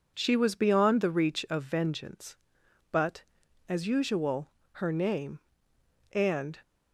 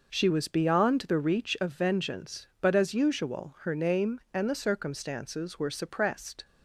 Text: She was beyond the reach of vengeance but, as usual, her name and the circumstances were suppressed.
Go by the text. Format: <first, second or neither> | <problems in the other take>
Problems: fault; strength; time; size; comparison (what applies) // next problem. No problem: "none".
second | stops before "the circumstances were suppressed"; at 6.6 s